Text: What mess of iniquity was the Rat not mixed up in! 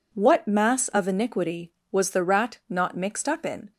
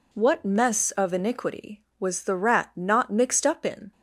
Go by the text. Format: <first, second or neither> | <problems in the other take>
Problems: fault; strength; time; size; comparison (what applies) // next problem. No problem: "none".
second | says "mass" for "mess"; at 0.4 s